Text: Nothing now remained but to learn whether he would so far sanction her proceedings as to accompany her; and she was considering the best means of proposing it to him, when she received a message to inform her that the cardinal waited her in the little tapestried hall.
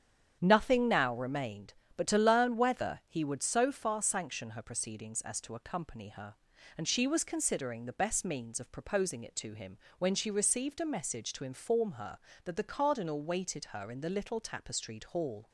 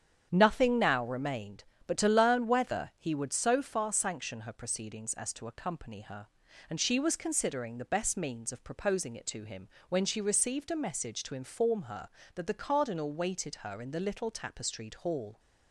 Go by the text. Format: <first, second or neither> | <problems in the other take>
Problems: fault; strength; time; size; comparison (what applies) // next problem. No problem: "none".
neither | starts louder than the rest; strong; the same in both